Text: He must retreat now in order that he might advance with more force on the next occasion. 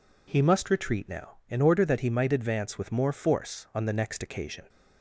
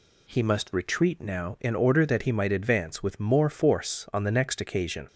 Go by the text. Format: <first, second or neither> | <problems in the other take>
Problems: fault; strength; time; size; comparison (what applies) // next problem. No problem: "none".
neither | none